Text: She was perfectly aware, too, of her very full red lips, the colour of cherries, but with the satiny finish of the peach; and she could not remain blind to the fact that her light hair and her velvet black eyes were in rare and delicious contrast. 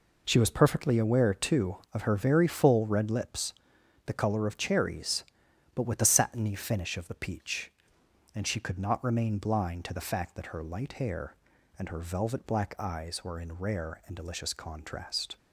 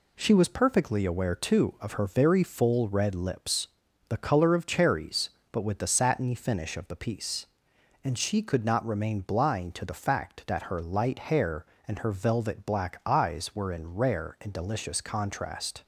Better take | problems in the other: first | says "piece" for "peach"; at 6.9 s

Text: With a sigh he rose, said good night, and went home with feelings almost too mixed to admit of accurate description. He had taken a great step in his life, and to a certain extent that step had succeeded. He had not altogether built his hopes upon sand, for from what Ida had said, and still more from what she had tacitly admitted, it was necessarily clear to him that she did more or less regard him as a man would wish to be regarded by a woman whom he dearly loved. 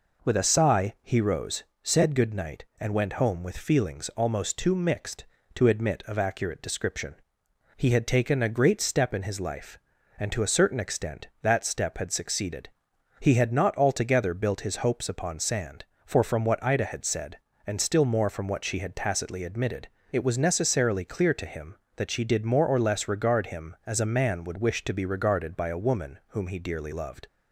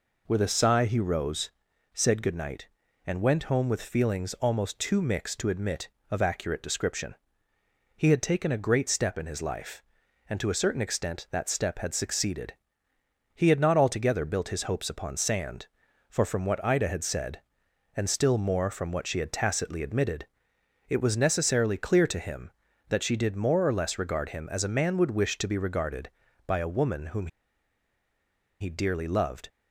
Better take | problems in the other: first | pauses between "whom" and "he"; strong; at 27.2 s; 1.3 s long

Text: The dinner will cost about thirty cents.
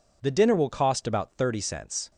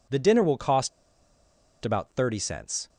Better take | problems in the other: first | pauses between "cost" and "about"; noticeable; at 0.8 s; 0.94 s long

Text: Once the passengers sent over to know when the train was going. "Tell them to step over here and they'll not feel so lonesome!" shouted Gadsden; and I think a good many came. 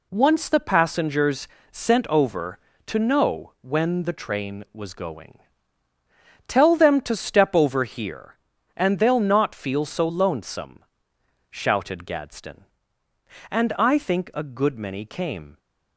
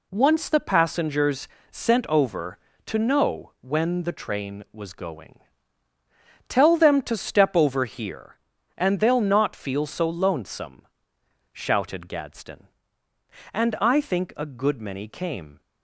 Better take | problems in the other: neither | pauses between "passengers" and "sent"; slight; the same in both

